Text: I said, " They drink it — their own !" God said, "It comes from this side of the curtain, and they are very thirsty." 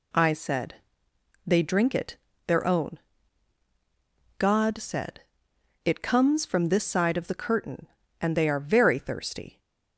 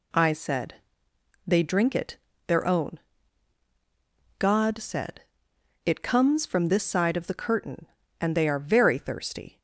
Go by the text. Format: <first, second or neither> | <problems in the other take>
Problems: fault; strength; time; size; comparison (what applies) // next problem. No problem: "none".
neither | none